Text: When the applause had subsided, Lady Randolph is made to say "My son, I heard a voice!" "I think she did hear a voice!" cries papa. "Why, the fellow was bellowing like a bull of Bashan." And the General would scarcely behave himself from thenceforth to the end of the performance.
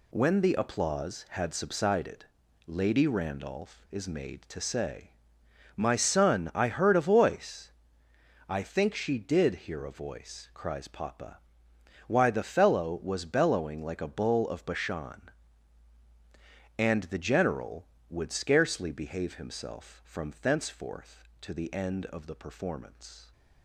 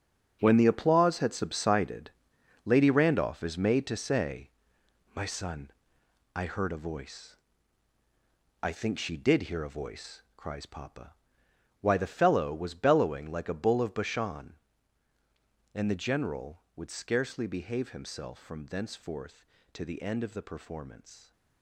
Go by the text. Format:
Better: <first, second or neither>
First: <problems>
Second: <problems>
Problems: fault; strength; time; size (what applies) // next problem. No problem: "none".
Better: first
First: pauses between "say" and "My"; noticeable; at 5.0 s; 0.66 s long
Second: gets quieter; strong; throughout; 12 dB // pauses between "say" and "My"; noticeable; at 4.5 s; 0.62 s long